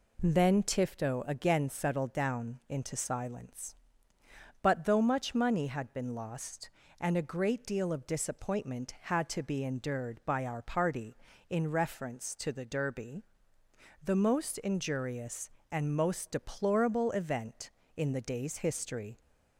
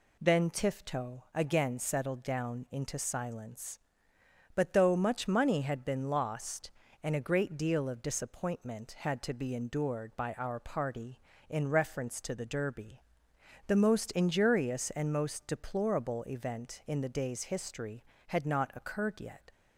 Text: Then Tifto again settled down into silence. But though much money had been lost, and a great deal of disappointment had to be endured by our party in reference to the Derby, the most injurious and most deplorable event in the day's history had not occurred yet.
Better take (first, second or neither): second